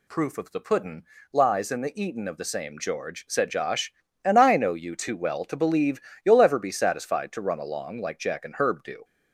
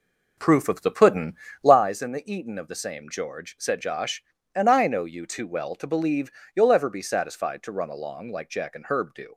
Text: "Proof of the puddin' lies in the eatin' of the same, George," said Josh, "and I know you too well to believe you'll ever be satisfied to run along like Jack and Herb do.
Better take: first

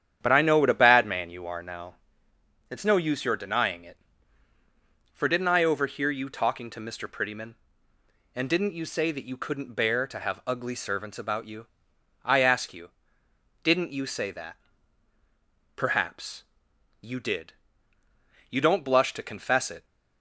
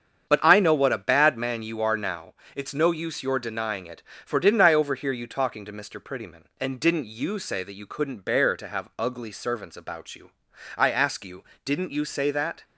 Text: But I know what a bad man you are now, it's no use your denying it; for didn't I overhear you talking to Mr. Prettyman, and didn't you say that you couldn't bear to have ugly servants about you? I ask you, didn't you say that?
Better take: second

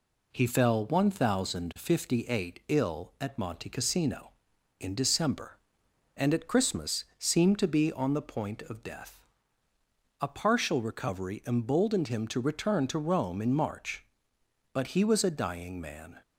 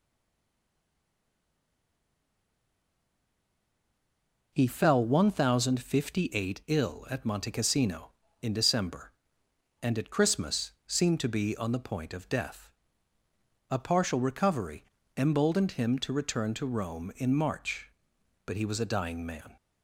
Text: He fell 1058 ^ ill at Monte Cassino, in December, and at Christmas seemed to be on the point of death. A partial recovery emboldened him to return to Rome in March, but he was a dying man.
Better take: first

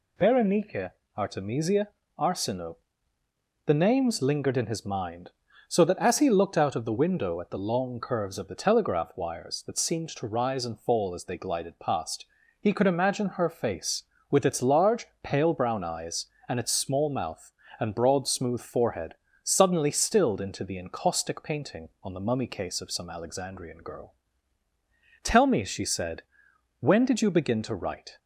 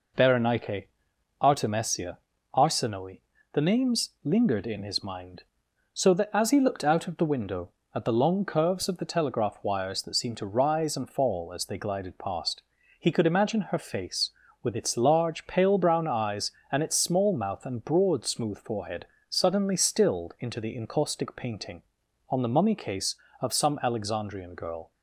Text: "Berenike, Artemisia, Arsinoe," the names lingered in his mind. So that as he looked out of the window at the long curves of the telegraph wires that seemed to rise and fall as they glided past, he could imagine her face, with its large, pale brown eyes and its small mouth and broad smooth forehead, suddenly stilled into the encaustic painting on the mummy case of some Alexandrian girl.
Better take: second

